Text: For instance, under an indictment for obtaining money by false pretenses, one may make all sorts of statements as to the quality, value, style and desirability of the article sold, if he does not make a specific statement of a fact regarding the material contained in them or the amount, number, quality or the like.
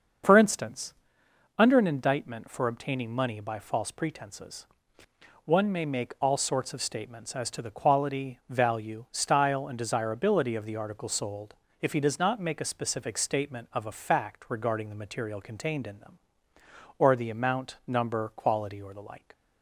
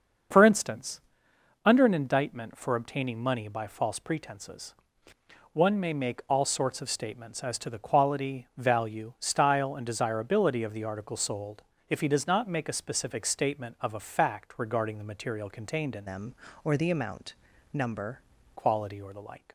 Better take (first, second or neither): first